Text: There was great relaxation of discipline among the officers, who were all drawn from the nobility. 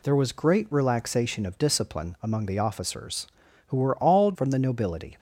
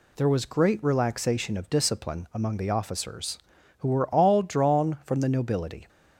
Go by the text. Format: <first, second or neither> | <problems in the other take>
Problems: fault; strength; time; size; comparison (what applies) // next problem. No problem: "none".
second | skips "drawn"; at 4.3 s